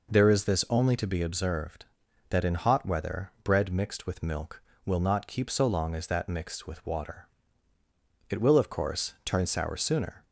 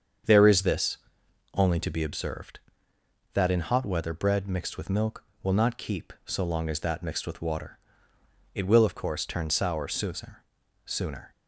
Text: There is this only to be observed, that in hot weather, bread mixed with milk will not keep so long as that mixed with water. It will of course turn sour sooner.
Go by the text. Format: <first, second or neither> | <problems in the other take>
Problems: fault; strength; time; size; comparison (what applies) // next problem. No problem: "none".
first | starts louder than the rest; strong; until 1.8 s; 7 dB // pauses between "this" and "only"; noticeable; at 0.9 s; 0.56 s long // says "sooner" twice; at 10.8 s